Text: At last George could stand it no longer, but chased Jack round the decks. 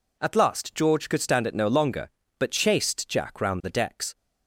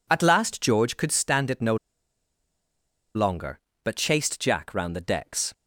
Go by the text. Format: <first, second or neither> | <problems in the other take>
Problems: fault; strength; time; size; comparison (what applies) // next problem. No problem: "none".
first | pauses between "no" and "longer"; strong; at 1.7 s; 1.3 s long